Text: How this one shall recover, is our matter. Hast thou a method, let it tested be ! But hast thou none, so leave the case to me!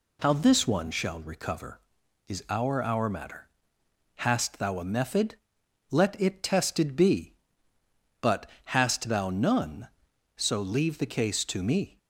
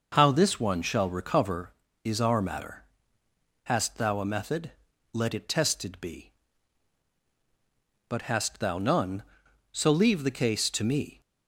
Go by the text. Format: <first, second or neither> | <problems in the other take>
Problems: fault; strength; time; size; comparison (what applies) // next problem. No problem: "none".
second | says "our" twice; at 2.8 s // pauses between "But" and "hast"; slight; at 8.4 s; 0.16 s long